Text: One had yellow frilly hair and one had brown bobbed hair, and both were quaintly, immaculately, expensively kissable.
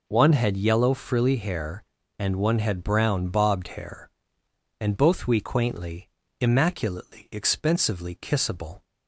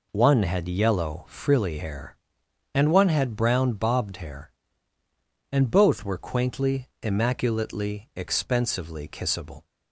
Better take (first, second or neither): second